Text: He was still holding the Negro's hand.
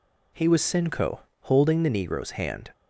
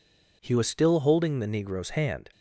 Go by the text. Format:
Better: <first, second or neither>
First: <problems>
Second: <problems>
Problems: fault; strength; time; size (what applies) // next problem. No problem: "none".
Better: second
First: says "sinco" for "still"; at 0.6 s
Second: none